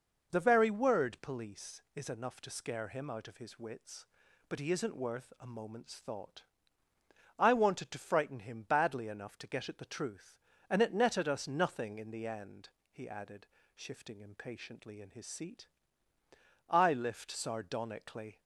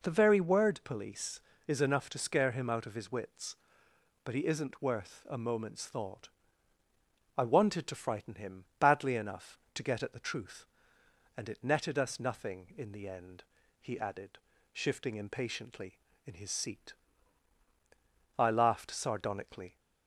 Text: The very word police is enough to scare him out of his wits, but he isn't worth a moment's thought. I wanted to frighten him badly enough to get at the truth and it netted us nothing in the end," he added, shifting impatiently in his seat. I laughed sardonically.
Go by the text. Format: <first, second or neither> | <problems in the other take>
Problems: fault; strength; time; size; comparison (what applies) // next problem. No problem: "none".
second | says "lift" for "laughed"; at 16.9 s